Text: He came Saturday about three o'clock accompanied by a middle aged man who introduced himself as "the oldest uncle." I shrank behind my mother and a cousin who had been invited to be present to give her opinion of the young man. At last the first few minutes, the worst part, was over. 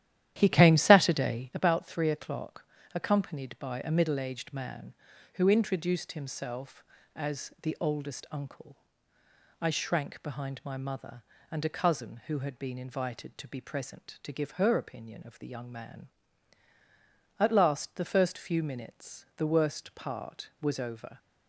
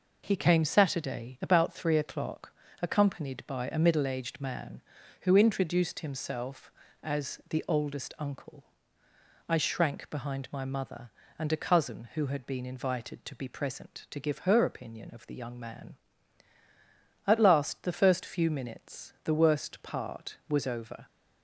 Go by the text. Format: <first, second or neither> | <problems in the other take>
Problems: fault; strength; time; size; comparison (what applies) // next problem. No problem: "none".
second | starts louder than the rest; strong; until 1.6 s; 12 dB // pauses between "o'clock" and "accompanied"; slight; at 2.6 s; 0.30 s long; slight in the second